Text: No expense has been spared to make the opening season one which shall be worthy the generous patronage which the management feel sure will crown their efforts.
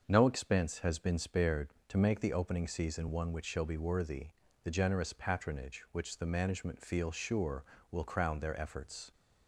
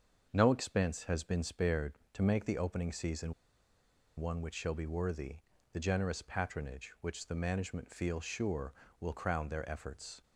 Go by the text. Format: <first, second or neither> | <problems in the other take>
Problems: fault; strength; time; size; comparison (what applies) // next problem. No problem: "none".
first | starts louder than the rest; until 1.3 s; 6.5 dB; also in the first // pauses between "season" and "one"; noticeable; at 3.3 s; 0.84 s long // pauses between "worthy" and "the"; slight; at 5.4 s; 0.34 s long; slight in the first